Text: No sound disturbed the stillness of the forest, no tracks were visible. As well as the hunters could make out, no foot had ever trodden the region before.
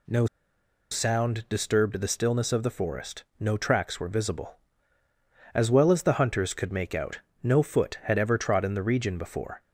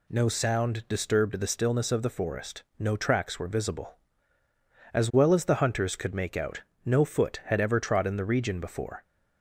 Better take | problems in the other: second | pauses between "No" and "sound"; noticeable; at 0.2 s; 0.65 s long

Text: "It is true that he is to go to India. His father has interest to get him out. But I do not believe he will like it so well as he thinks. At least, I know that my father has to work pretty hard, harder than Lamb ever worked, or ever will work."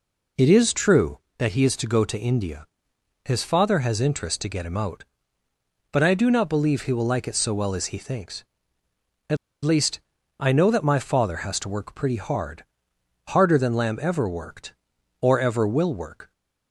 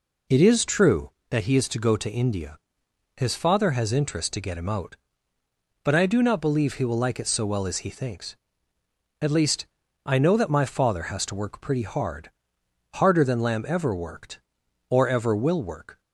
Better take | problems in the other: second | pauses between "At" and "least"; slight; at 9.3 s; 0.28 s long

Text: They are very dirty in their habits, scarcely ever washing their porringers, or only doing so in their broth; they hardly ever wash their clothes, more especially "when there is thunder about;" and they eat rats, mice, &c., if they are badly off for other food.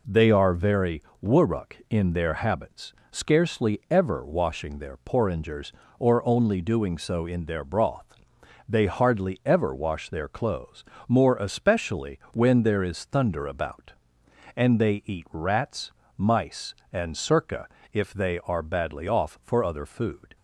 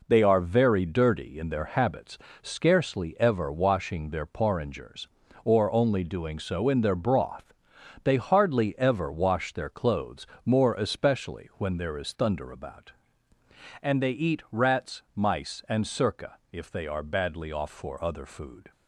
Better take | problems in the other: second | says "wurruk" for "dirty"; at 1.1 s

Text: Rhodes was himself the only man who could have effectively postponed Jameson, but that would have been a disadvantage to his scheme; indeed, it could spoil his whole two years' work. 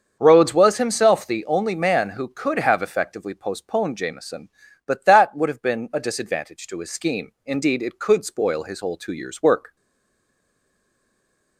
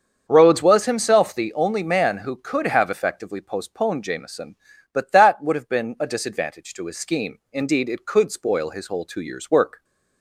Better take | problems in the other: second | starts louder than the rest; until 1.1 s; 7 dB; also in the second // stays silent after the last word; noticeable; from 9.7 s on; 1.8 s long

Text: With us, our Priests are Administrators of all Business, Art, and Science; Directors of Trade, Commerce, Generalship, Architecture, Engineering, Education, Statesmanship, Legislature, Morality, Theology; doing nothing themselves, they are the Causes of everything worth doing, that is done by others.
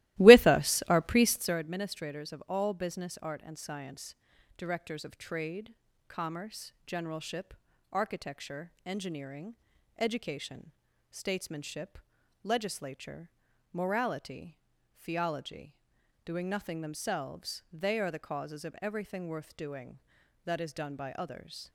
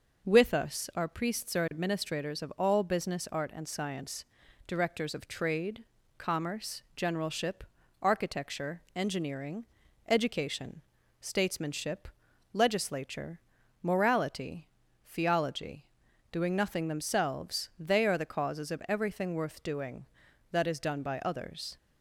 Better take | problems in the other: second | starts louder than the rest; strong; until 1.6 s; 17 dB

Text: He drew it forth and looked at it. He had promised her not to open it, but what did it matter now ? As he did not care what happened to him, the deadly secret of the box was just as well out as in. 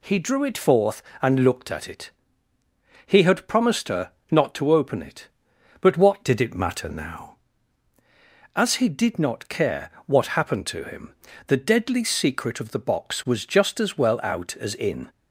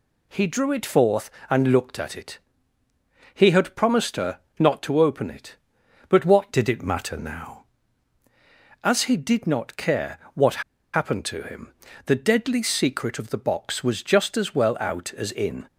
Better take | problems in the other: first | pauses between "her" and "not"; slight; at 4.3 s; 0.22 s long; slight in the first // pauses between "care" and "what"; slight; at 10.1 s; 0.16 s long; slight in the first // pauses between "what" and "happened"; slight; at 10.6 s; 0.33 s long

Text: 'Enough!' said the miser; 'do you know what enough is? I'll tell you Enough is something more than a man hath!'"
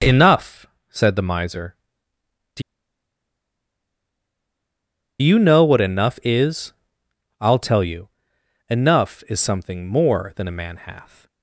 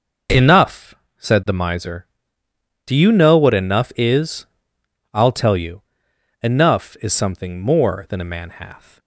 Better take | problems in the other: second | pauses between "do" and "you"; strong; at 2.6 s; 2.6 s long // pauses between "you" and "Enough"; noticeable; at 8.1 s; 0.58 s long; noticeable in the second

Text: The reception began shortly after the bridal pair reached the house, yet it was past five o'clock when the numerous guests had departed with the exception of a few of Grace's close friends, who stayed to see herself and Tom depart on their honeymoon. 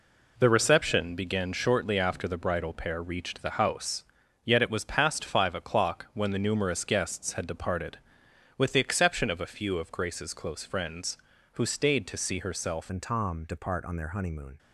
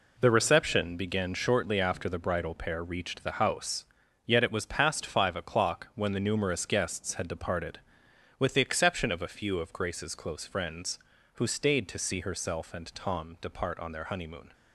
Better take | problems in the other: second | changes voice at "and"; from 12.8 s on; 1.7 s long

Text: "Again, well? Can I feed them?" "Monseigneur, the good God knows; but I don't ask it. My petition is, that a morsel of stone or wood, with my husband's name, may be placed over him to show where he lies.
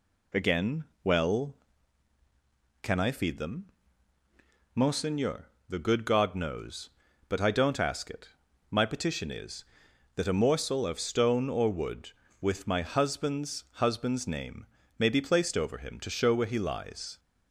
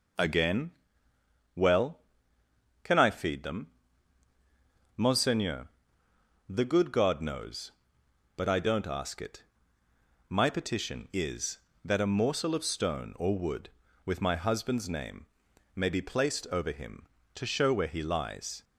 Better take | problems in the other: second | says "husband's" twice; at 13.7 s

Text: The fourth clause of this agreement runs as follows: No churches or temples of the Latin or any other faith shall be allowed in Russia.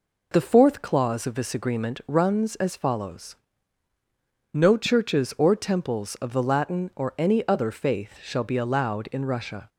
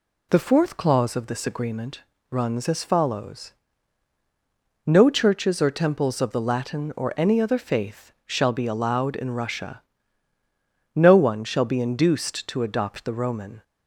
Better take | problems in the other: first | pauses between "agreement" and "runs"; slight; at 2.0 s; 0.26 s long // pauses between "faith" and "shall"; slight; at 8.1 s; 0.16 s long // goes on to say "No one shall be induced to adopt the Roman"; strong; from 10.9 s on; 2.6 s long

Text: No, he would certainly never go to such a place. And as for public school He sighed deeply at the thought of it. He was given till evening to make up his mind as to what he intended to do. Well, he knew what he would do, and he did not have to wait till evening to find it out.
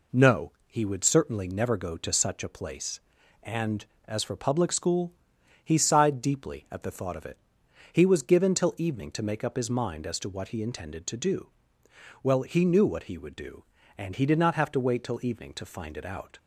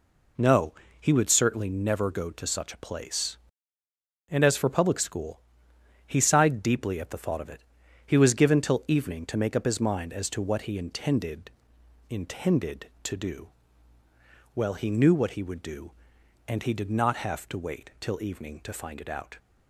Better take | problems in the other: first | pauses between "school" and "He"; noticeable; at 5.4 s; 0.66 s long; noticeable in the first // says "intended" twice; at 12.0 s

